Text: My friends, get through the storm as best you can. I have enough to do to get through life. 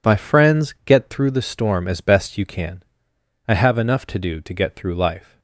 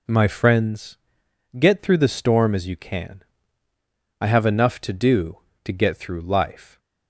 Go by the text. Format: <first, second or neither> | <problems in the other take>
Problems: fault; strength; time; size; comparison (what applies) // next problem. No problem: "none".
first | skips "best"; at 2.6 s